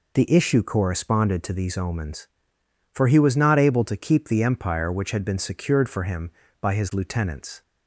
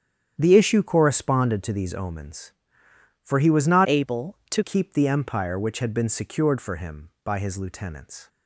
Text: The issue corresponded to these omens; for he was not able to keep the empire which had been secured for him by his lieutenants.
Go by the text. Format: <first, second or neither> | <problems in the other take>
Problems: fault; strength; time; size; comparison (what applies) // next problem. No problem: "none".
first | starts louder than the rest; strong; until 1.3 s; 9 dB // changes voice from "able" to "to"; from 3.8 to 4.6 s; 0.8 s long